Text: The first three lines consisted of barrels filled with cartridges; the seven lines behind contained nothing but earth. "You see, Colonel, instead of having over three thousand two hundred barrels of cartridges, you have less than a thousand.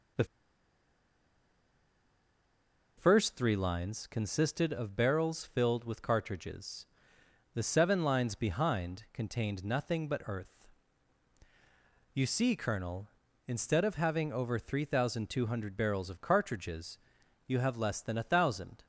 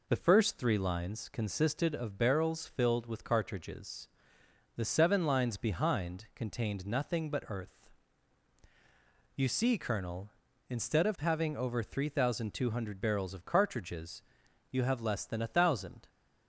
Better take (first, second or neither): second